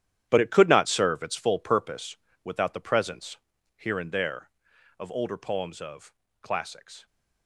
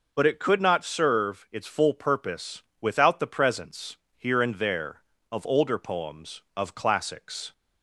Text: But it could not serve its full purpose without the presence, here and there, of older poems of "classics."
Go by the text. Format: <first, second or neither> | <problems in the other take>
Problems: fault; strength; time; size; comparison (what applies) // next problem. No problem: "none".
second | gets quieter; strong; throughout; 12.5 dB // pauses between "purpose" and "without"; slight; at 2.1 s; 0.26 s long; slight in the second // pauses between "of" and "classics"; slight; at 6.1 s; 0.28 s long